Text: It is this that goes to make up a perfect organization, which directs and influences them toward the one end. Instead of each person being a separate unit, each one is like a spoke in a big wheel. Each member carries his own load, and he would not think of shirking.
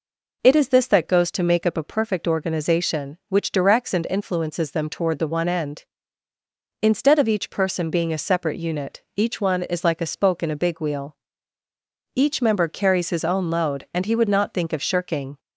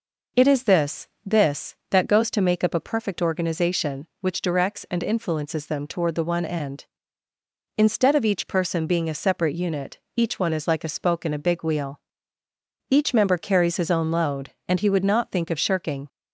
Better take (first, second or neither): first